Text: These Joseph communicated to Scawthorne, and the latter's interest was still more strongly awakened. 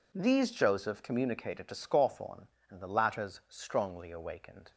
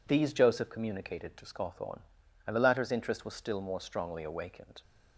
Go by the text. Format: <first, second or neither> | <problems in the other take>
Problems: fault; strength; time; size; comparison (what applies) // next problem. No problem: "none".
second | skips "interest was still more"; at 3.4 s